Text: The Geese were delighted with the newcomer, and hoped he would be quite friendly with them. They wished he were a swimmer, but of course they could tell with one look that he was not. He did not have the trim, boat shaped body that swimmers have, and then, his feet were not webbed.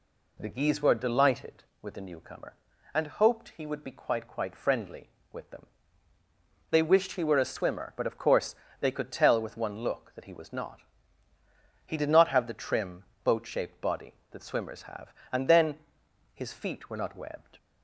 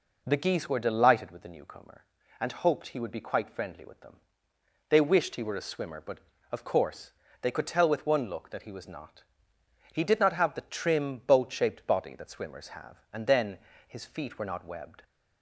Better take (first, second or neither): second